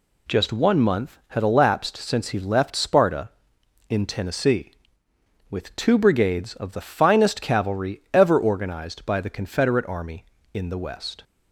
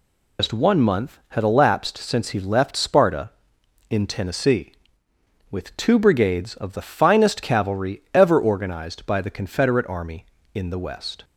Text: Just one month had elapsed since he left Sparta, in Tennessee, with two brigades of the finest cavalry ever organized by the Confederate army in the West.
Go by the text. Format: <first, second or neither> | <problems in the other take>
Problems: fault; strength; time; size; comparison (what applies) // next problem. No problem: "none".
first | loses the start of "Just"; at 0.3 s; 115 ms